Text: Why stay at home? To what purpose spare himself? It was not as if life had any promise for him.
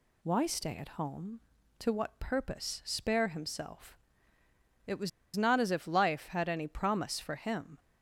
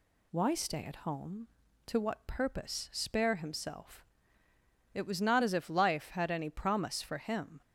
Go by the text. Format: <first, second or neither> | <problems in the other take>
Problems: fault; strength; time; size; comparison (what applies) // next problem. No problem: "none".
second | pauses between "was" and "not"; slight; at 5.0 s; 0.26 s long